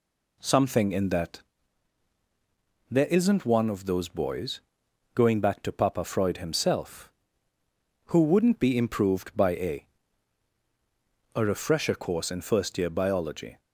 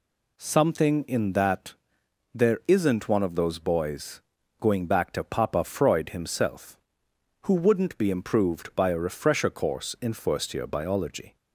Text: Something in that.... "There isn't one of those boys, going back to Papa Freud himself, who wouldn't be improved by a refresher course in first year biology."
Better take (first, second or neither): second